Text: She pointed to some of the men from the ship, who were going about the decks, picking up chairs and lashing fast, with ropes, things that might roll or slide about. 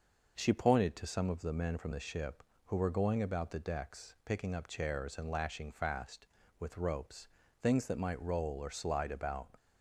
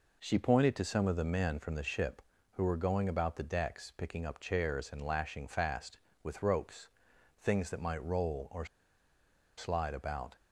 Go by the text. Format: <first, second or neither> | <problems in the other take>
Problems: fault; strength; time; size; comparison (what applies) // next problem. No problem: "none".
first | pauses between "or" and "slide"; noticeable; at 8.6 s; 0.91 s long